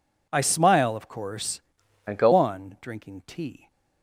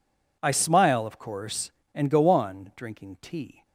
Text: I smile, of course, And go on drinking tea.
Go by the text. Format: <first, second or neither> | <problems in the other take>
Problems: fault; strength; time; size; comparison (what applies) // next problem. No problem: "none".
second | changes voice from "And" to "go"; from 2.0 to 2.3 s; 0.3 s long